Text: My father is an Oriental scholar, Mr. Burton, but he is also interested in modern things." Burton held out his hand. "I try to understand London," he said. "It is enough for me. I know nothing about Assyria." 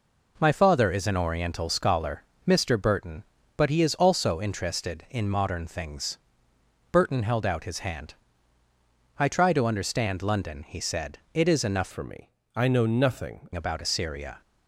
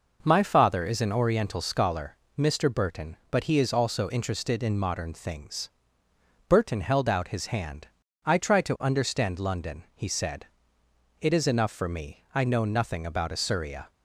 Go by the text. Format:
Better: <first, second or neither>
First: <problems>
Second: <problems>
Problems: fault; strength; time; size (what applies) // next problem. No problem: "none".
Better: second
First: changes voice from "for" to "nothing"; from 11.9 to 13.4 s; 1.5 s long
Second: none